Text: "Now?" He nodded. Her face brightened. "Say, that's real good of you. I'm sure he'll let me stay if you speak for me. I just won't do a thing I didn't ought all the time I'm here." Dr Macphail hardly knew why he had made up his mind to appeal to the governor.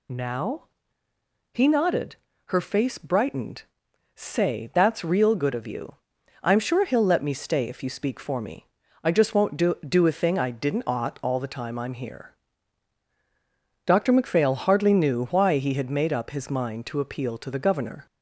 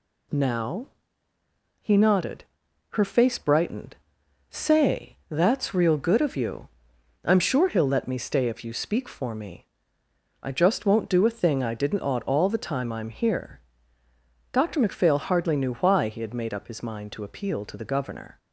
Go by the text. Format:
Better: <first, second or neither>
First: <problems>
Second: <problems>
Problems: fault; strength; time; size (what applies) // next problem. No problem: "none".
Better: second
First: says "do" twice; at 9.8 s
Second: none